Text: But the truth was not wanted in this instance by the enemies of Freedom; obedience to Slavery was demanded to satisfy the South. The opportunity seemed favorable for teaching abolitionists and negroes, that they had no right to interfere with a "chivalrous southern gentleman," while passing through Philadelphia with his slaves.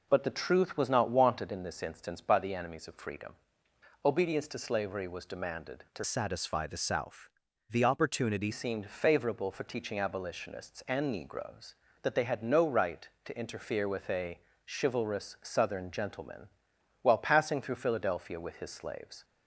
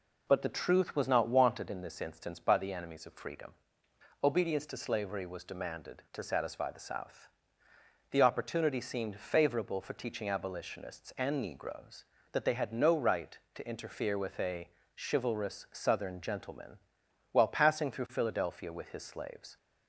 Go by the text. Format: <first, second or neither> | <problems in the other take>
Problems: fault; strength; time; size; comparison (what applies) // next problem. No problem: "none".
second | changes voice from "satisfy" to "opportunity"; from 6.0 to 8.5 s; 2.5 s long // pauses between "a" and "chivalrous"; slight; at 14.3 s; 0.30 s long; slight in the second